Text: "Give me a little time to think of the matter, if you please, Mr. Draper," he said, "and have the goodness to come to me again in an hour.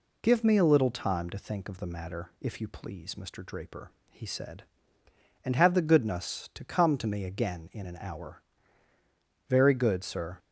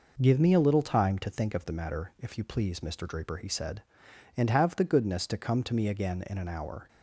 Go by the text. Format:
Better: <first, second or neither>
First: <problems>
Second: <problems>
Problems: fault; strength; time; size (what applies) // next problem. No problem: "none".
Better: second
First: goes on to say "Very good sir"; noticeable; from 9.4 s on; 0.90 s long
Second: none